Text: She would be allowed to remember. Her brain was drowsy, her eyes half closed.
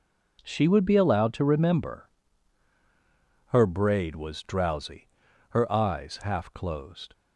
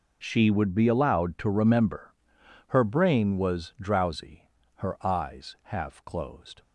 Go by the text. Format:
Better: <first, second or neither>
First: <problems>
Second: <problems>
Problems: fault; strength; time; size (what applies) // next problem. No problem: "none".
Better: second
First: says "braid" for "brain"; at 3.6 s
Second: none